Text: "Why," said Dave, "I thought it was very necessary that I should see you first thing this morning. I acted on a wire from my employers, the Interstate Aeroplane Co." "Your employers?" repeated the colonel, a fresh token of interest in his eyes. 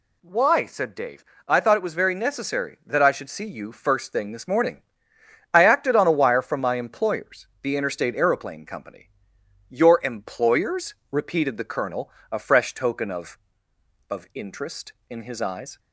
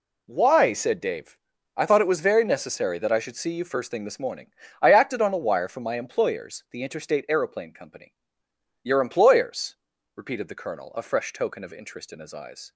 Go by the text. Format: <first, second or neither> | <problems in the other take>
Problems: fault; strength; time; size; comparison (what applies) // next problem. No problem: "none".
second | says "of" twice; at 14.1 s